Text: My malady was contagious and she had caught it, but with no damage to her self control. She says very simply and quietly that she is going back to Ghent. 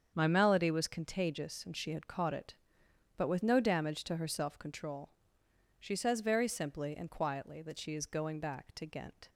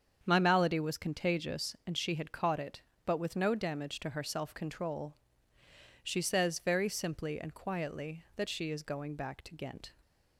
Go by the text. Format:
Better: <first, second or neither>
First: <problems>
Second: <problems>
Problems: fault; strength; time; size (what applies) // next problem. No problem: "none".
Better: neither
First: starts louder than the rest; strong; until 1.1 s; 7.5 dB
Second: starts louder than the rest; strong; until 1.2 s; 7 dB